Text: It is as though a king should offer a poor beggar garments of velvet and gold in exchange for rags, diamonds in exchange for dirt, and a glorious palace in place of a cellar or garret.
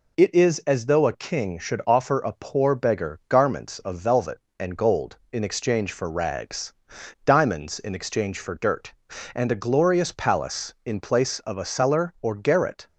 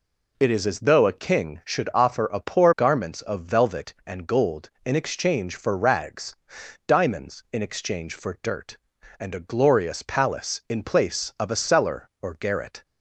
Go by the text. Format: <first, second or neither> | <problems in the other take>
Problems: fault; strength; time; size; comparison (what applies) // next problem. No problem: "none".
first | skips "beggar"; at 2.7 s